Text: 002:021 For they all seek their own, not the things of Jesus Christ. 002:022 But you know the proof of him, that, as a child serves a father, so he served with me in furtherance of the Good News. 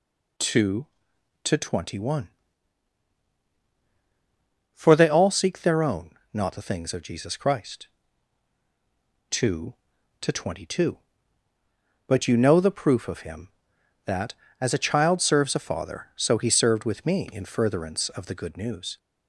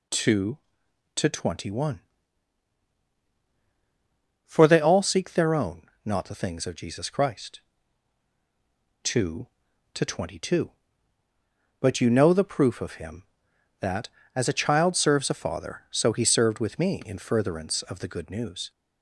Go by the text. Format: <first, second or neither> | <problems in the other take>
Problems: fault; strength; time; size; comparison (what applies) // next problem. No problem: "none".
neither | none